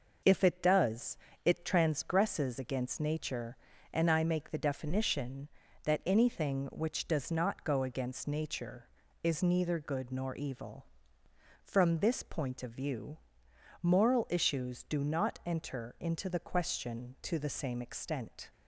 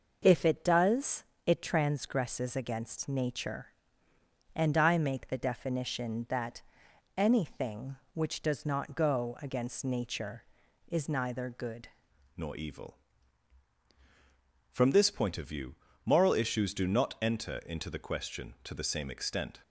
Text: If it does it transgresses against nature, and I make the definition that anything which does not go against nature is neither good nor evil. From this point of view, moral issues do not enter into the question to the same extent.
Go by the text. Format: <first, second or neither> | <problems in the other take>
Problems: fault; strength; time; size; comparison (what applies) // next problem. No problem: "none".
first | pauses between "does" and "it"; slight; at 1.2 s; 0.20 s long; slight in the first // pauses between "that" and "anything"; noticeable; at 6.6 s; 0.56 s long // changes voice at "nor"; from 12.3 s on; 7.3 s long